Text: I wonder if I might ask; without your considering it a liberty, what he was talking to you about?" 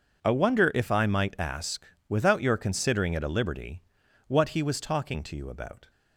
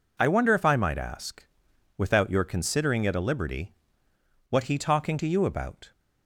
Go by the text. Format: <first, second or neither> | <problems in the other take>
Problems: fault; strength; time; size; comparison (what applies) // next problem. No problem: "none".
first | skips "was"; at 4.7 s